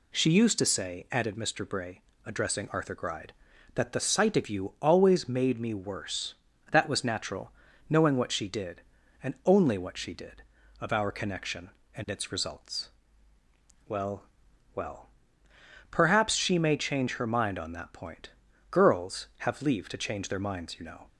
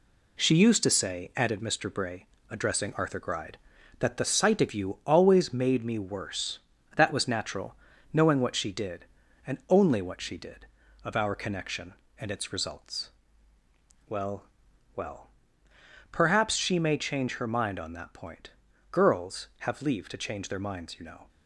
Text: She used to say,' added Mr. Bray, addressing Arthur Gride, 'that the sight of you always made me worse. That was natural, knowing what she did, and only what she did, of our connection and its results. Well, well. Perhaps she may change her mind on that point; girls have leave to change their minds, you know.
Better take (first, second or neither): first